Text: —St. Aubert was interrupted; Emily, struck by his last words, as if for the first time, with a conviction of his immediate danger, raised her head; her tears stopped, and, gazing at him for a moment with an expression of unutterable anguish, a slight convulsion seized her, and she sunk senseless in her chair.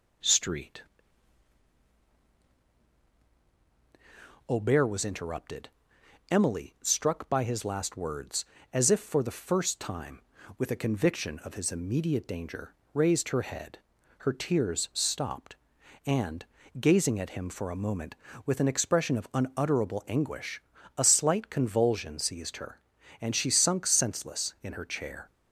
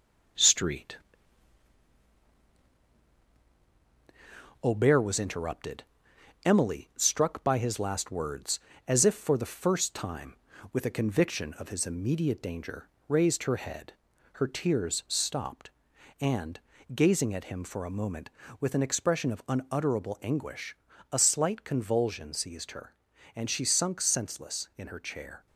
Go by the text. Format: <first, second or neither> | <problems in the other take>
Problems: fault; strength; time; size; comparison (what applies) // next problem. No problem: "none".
first | gets quieter; slight; throughout; 3 dB